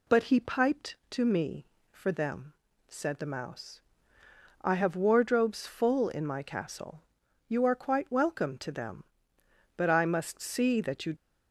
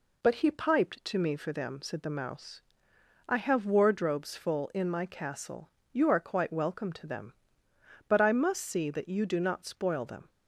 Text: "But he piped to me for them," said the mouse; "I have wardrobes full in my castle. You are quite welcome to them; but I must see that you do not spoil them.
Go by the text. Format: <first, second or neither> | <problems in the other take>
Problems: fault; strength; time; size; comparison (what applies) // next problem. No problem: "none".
second | stops before "do not spoil them"; at 11.1 s